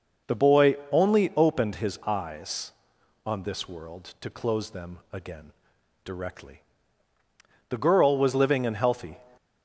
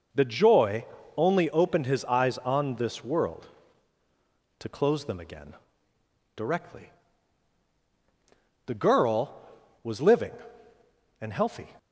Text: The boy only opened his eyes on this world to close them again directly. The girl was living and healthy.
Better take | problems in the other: first | says "joy" for "boy"; at 0.2 s // pauses between "again" and "directly"; noticeable; at 5.5 s; 0.80 s long; noticeable in the first

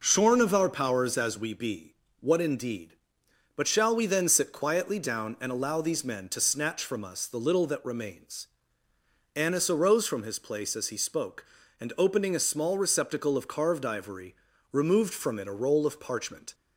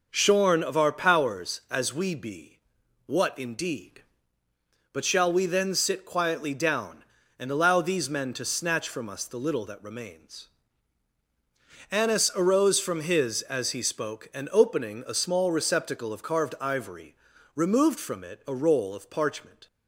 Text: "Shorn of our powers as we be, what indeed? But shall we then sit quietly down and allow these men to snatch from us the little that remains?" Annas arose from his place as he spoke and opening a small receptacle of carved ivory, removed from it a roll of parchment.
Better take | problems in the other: first | skips "place"; at 13.4 s

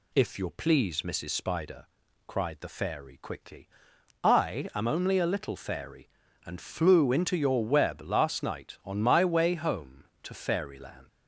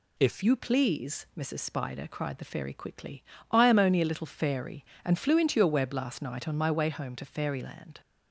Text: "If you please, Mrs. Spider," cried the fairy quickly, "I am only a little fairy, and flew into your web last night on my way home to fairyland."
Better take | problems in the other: first | changes voice at "you"; from 0.4 s on; 7.6 s long

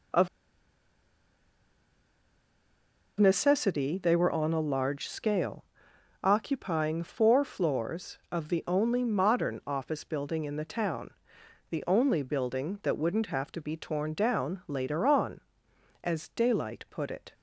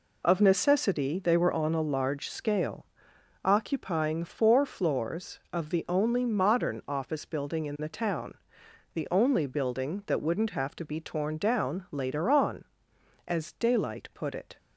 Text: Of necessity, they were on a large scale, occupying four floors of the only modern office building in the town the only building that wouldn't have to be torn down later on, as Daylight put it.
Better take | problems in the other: second | pauses between "Of" and "necessity"; strong; at 0.2 s; 2.8 s long // pauses between "town" and "the"; noticeable; at 11.0 s; 0.60 s long; noticeable in the second

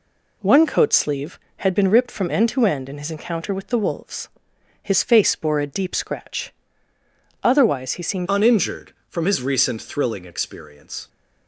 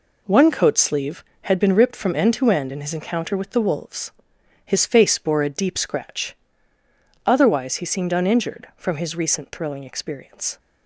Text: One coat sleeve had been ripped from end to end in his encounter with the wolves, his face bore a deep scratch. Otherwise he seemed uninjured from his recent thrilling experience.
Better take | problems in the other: second | changes voice at "uninjured"; from 8.2 s on; 2.8 s long

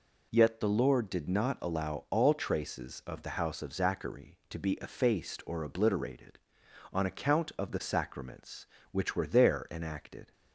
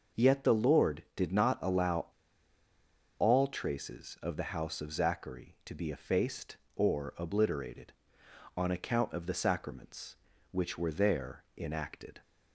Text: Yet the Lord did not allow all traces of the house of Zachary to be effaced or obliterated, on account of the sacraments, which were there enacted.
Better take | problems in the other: first | pauses between "allow" and "all"; at 2.0 s; 1.1 s long // pauses between "there" and "enacted"; slight; at 11.4 s; 0.16 s long

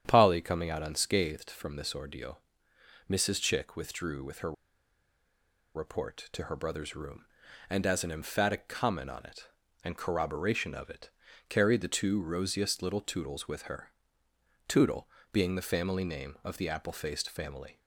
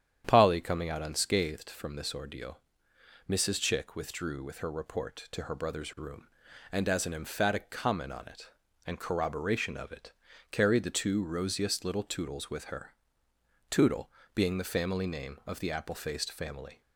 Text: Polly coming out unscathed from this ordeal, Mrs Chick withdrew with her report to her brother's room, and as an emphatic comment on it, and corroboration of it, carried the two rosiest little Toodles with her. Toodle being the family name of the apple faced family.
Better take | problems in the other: second | starts louder than the rest; strong; until 1.0 s; 9 dB; strong in the second // pauses between "her" and "report"; at 4.5 s; 1.2 s long // pauses between "Toodle" and "being"; slight; at 15.0 s; 0.24 s long; slight in the second

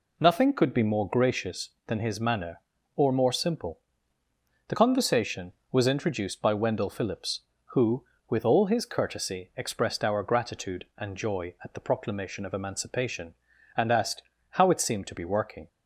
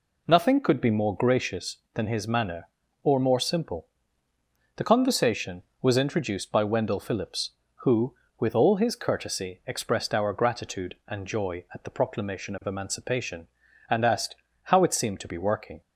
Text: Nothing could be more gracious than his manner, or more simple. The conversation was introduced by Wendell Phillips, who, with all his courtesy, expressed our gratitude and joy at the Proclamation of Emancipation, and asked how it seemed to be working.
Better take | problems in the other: neither | pauses between "asked" and "how"; slight; the same in both

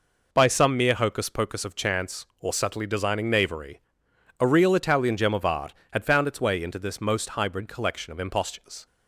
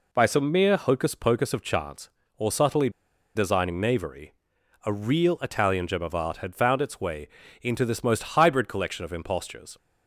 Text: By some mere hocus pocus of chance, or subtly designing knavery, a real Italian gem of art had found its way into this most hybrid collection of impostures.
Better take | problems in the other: first | pauses between "subtly" and "designing"; at 2.8 s; 0.45 s long // pauses between "way" and "into"; slight; at 7.2 s; 0.34 s long

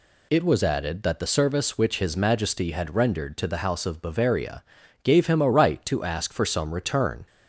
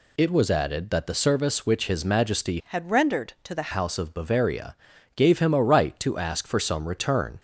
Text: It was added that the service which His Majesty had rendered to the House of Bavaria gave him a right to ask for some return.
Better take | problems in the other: first | changes voice from "had" to "the"; from 2.6 to 3.7 s; 1.1 s long // pauses between "Bavaria" and "gave"; at 4.7 s; 0.40 s long; also in the first

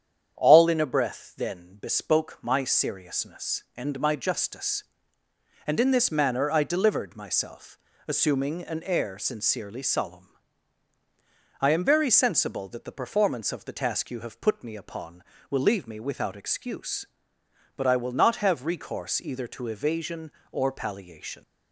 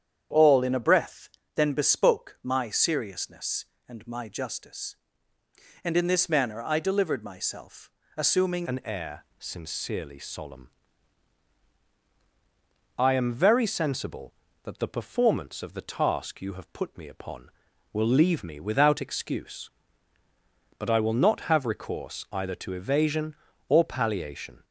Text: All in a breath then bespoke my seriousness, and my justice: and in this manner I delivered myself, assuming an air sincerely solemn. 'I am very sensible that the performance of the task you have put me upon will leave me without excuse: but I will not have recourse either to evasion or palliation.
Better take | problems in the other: first | starts louder than the rest; strong; until 1.6 s; 9 dB; strong in the first // pauses between "breath" and "then"; slight; at 1.2 s; 0.28 s long // changes voice at "an"; from 8.6 s on; 16.0 s long

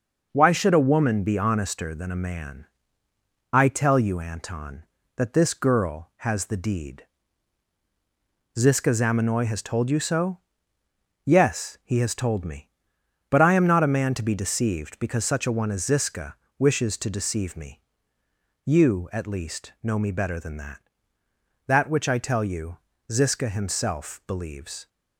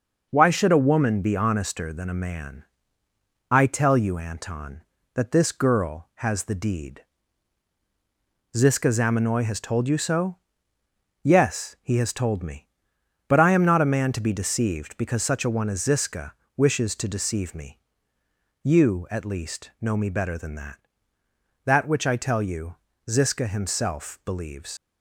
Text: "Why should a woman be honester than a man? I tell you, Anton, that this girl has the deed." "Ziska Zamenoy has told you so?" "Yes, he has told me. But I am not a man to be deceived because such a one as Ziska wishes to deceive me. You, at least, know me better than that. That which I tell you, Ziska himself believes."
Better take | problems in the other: first | pauses between "Ziska" and "wishes"; slight; at 16.3 s; 0.22 s long; slight in the first // leaves "believes" unfinished; at 24.7 s; 90 ms

